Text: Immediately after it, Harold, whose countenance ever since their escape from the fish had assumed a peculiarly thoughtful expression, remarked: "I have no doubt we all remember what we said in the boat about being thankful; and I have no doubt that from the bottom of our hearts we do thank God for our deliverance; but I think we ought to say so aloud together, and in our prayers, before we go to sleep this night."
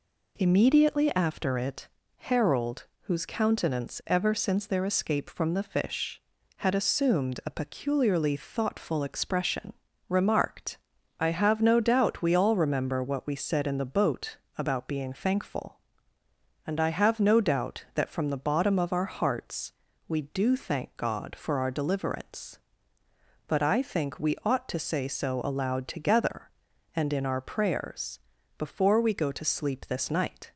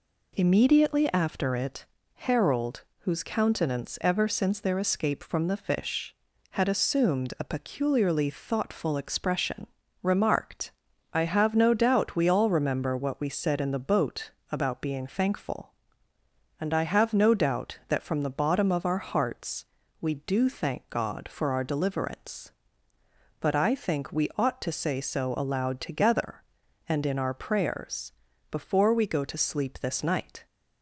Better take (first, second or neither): neither